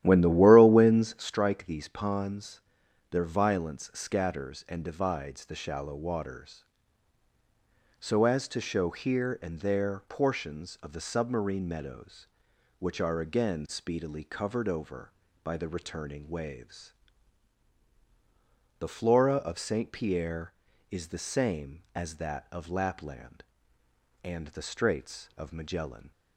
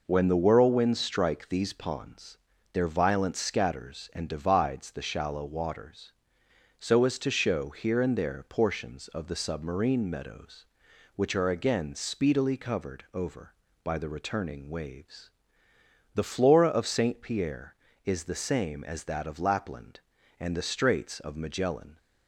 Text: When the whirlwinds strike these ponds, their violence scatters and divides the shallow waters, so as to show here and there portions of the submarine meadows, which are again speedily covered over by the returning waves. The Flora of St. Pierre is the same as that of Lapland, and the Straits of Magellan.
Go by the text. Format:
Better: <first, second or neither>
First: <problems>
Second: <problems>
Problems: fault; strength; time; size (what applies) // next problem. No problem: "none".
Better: second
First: starts louder than the rest; strong; until 1.4 s; 12.5 dB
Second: none